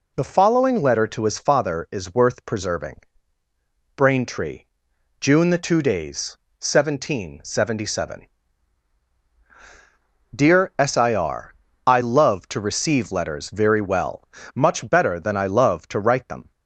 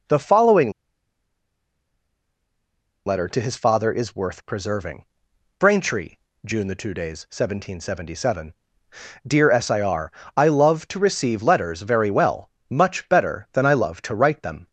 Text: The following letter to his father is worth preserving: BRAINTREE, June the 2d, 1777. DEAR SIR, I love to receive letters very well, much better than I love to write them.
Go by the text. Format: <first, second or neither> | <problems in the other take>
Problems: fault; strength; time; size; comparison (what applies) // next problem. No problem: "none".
first | pauses between "following" and "letter"; strong; at 0.6 s; 2.3 s long